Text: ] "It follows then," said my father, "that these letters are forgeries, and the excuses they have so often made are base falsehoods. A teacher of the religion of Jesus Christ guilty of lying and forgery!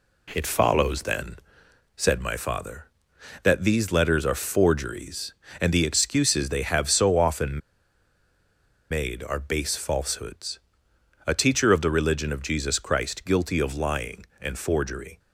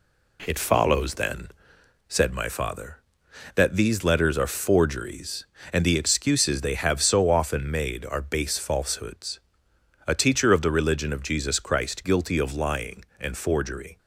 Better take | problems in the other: second | pauses between "often" and "made"; strong; at 7.5 s; 1.3 s long

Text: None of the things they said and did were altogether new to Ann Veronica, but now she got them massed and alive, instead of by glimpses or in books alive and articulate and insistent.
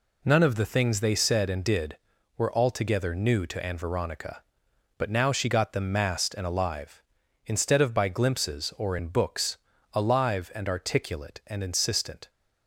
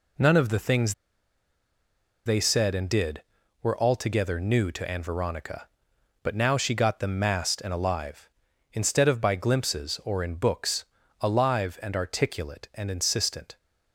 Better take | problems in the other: first | pauses between "things" and "they"; strong; at 0.9 s; 1.3 s long // pauses between "books" and "alive"; slight; at 10.8 s; 0.36 s long; slight in the first

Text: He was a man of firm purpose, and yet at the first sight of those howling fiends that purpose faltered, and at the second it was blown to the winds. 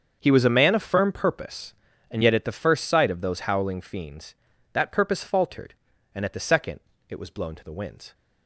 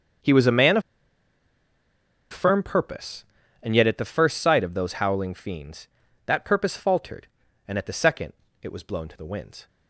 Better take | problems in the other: first | starts louder than the rest; until 2.7 s; 7 dB; also in the first // pauses between "of" and "firm"; strong; at 0.8 s; 1.5 s long // pauses between "second" and "it"; slight; at 8.3 s; 0.28 s long; slight in the first

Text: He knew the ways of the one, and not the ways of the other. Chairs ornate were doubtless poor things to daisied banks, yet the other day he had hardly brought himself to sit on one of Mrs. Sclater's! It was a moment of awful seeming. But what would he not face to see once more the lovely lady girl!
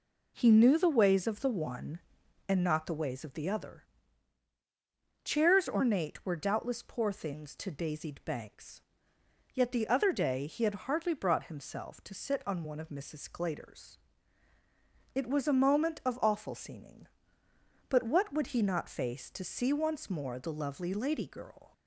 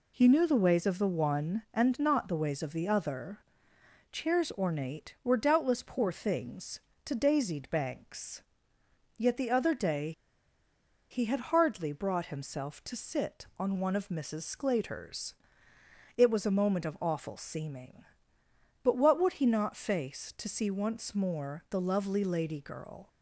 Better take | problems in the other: first | pauses between "day" and "he"; at 10.1 s; 0.99 s long

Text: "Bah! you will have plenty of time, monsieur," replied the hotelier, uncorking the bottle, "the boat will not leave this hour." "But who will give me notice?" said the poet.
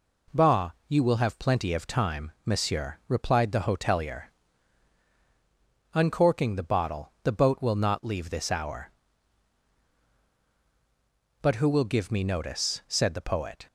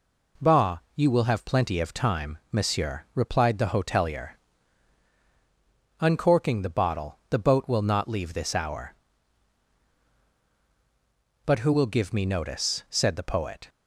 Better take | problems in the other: neither | none

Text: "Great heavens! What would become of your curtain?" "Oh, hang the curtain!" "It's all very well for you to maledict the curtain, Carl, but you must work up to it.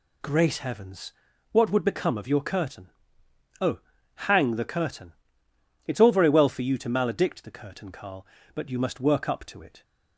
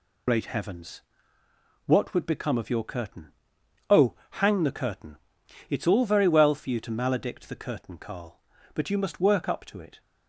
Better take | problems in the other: first | loses the start of "Great"; at 0.2 s; 80 ms

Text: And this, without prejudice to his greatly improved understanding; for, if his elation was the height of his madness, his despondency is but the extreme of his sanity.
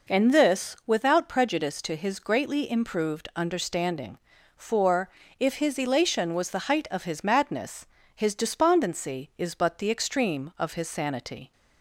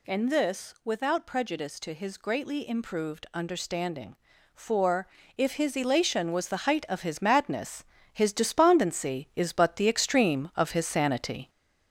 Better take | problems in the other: first | gets louder; slight; throughout; 3.5 dB

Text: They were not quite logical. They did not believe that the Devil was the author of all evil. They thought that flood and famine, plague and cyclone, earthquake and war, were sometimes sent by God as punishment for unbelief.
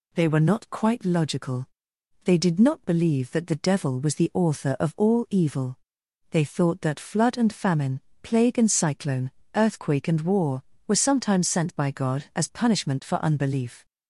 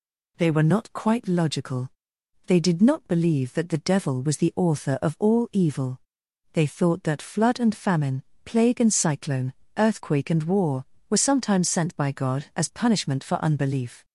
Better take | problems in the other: neither | none

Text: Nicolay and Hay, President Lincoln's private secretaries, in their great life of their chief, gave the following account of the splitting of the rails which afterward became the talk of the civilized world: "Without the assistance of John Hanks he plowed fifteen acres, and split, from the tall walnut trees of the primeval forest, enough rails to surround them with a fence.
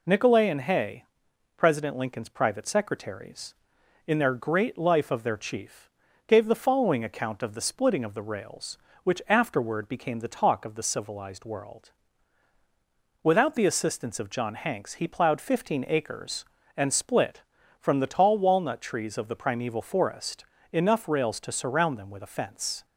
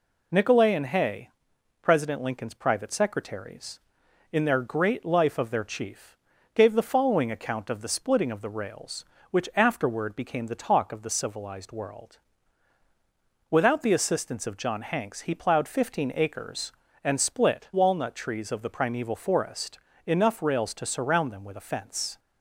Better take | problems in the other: first | skips "from the tall"; at 17.7 s

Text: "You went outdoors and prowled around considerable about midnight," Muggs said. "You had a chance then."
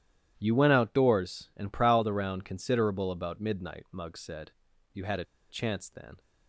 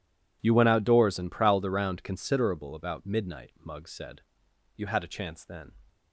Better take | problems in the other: second | starts louder than the rest; strong; until 1.3 s; 11.5 dB // pauses between "a" and "chance"; slight; at 5.2 s; 0.24 s long

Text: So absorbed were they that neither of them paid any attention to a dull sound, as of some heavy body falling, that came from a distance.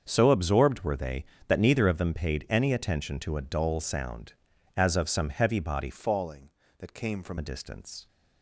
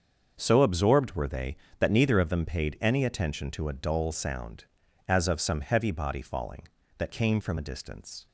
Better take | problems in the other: second | starts louder than the rest; until 1.0 s; 7 dB; also in the second // changes voice from "falling" to "from"; from 5.9 to 7.3 s; 1.4 s long

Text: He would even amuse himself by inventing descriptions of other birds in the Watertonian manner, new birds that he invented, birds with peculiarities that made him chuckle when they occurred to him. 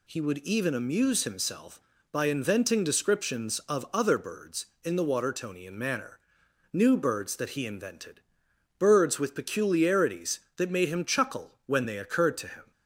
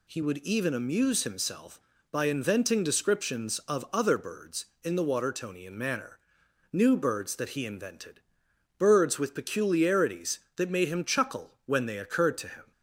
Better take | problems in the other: neither | none

